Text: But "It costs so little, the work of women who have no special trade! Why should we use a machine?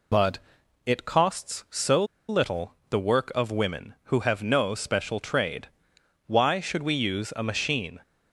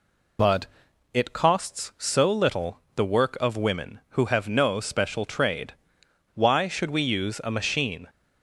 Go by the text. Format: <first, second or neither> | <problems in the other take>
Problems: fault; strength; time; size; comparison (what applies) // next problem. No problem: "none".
second | pauses between "But" and "It"; noticeable; at 0.3 s; 0.48 s long; noticeable in the second // pauses between "so" and "little"; slight; at 2.0 s; 0.24 s long